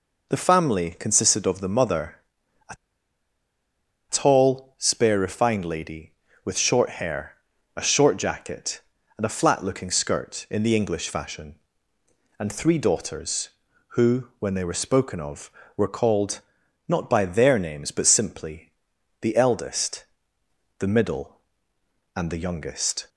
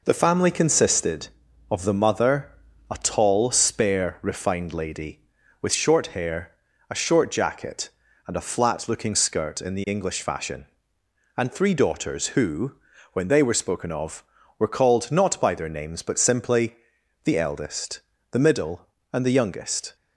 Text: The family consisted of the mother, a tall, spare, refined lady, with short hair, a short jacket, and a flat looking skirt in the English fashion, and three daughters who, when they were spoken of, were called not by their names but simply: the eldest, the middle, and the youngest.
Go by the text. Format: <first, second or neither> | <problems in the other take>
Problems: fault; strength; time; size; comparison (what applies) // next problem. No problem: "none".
second | pauses between "a" and "tall"; strong; at 2.7 s; 1.3 s long // pauses between "called" and "not"; noticeable; at 16.3 s; 0.48 s long